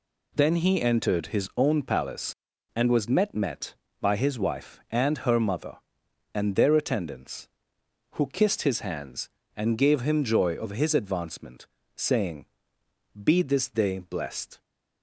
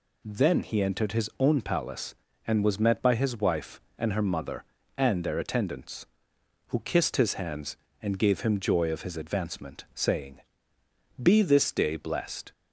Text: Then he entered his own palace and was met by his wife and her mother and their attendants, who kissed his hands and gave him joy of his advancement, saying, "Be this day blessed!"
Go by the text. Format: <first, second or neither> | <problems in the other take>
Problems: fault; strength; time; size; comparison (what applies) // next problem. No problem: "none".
second | says "met" twice; at 3.3 s